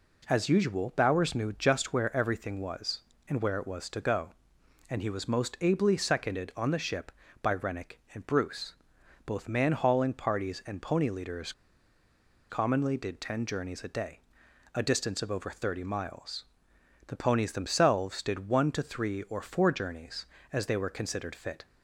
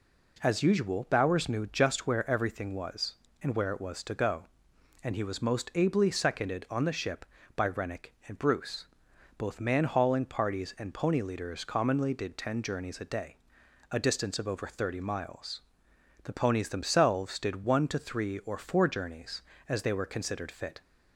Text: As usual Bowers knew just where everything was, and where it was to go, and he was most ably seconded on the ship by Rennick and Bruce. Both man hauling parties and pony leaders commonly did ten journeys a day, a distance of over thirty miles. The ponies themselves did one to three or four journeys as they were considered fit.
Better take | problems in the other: second | pauses between "leaders" and "commonly"; at 11.5 s; 0.98 s long

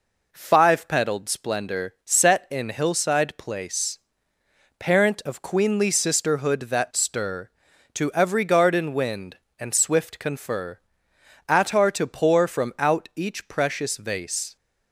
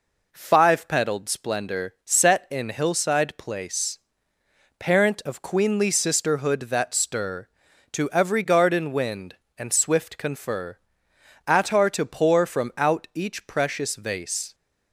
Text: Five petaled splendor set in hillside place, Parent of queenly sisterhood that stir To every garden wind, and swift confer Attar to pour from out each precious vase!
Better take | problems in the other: neither | pauses between "confer" and "Attar"; noticeable; the same in both

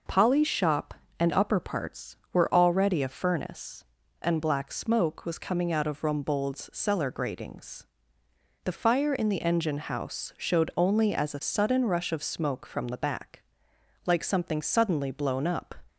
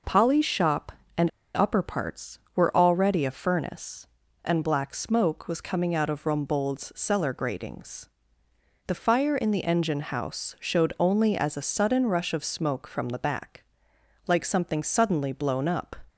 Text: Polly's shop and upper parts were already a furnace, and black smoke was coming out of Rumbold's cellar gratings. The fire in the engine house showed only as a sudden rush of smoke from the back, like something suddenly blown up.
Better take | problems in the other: first | pauses between "and" and "upper"; slight; at 1.2 s; 0.25 s long

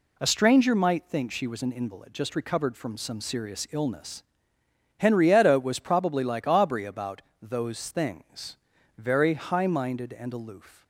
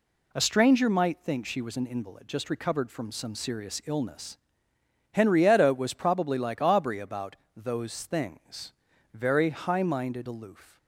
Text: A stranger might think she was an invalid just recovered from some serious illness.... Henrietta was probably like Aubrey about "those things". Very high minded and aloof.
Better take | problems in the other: first | pauses between "about" and "those"; slight; at 7.3 s; 0.22 s long; slight in the first // skips "and"; at 10.2 s

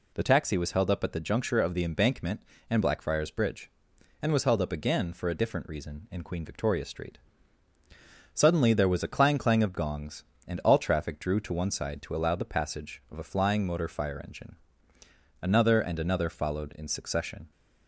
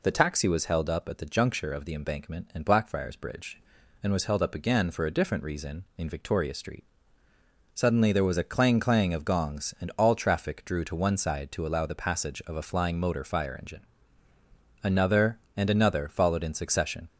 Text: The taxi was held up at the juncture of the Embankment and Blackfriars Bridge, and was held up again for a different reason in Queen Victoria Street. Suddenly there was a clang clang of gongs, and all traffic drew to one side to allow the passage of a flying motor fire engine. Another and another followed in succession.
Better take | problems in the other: first | skips "Queen"; at 6.0 s

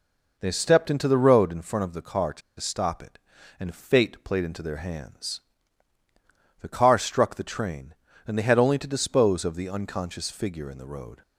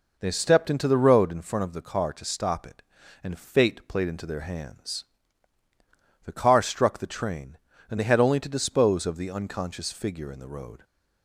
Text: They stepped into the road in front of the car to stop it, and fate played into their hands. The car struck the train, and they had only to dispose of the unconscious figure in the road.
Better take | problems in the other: second | pauses between "to" and "stop"; slight; at 2.4 s; 0.18 s long

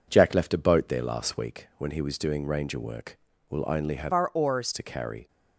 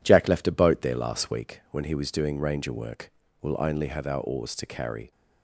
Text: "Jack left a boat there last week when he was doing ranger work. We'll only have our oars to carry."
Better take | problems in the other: second | changes voice from "our" to "oars"; from 4.1 to 4.7 s; 0.6 s long

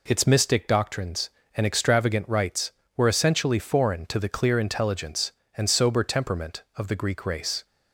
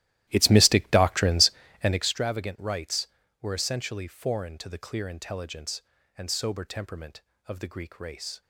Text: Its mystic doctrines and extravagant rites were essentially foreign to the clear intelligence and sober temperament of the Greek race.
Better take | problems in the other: first | starts louder than the rest; strong; until 2.1 s; 15 dB

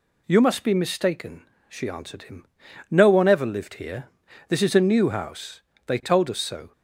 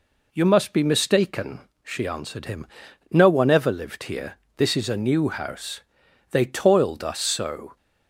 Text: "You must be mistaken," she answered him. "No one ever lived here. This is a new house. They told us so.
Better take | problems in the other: first | says "toiled" for "told"; at 6.4 s

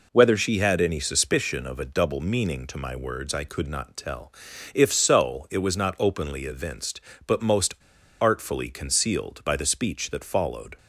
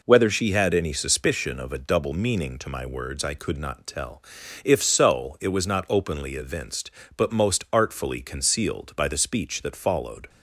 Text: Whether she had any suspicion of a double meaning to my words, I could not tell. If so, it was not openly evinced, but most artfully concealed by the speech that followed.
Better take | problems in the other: second | pauses between "most" and "artfully"; noticeable; at 7.7 s; 0.46 s long

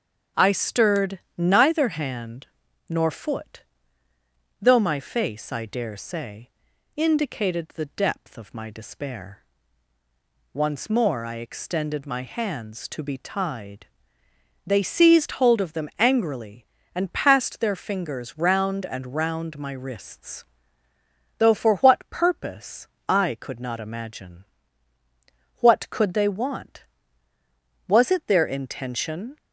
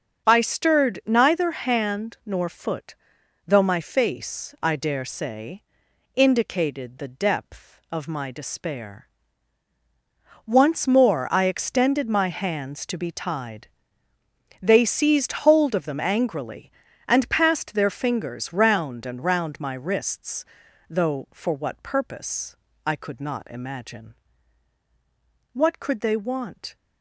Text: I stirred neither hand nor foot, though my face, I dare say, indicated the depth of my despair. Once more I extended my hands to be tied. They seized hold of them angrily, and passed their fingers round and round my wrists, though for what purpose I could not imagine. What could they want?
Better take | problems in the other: second | starts louder than the rest; until 1.5 s; 7 dB; also in the second // pauses between "stirred" and "neither"; slight; at 1.2 s; 0.16 s long // pauses between "hand" and "nor"; at 2.4 s; 0.42 s long // pauses between "purpose" and "I"; slight; at 22.8 s; 0.20 s long; slight in the second // goes on to say "Was it their intention"; from 27.8 s on; 1.5 s long

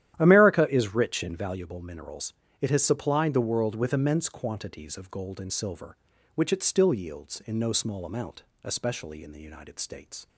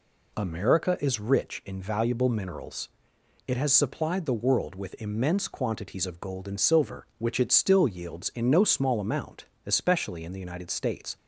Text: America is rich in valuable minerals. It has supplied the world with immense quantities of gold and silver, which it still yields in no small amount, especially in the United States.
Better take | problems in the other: second | starts louder than the rest; strong; until 1.7 s; 11.5 dB

